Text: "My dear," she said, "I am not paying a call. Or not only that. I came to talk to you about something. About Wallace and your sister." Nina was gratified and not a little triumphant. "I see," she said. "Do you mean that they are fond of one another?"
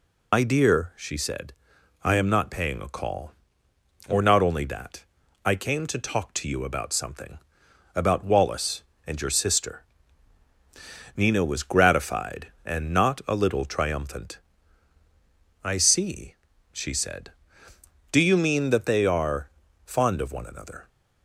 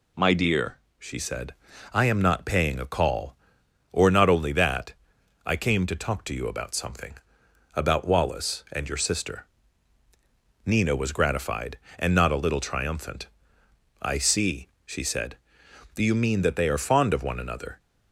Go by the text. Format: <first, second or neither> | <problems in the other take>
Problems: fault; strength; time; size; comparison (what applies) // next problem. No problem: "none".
second | loses the start of "My"; at 0.3 s; 85 ms // pauses between "are" and "fond"; slight; at 19.4 s; 0.36 s long